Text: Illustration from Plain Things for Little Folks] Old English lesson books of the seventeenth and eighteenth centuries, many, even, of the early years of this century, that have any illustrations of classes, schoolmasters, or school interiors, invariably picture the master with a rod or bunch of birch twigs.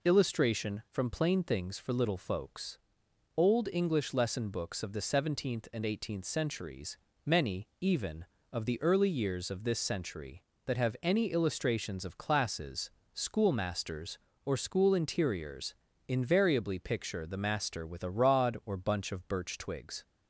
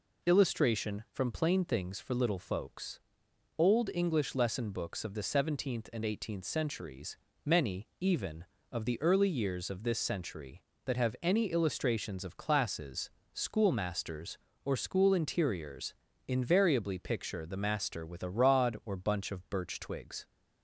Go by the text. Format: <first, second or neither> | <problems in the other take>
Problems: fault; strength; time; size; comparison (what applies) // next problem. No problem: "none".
neither | pauses between "Folks" and "Old"; noticeable; the same in both